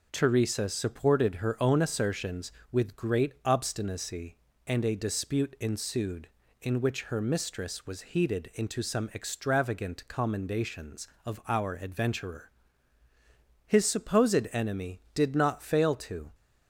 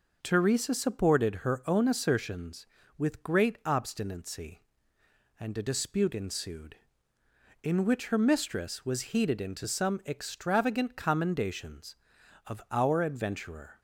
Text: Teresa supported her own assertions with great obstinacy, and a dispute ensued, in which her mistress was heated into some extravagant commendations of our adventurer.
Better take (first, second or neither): second